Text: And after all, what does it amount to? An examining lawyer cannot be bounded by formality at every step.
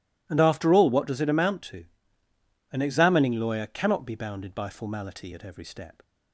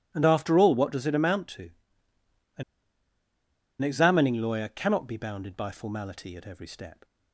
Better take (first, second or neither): first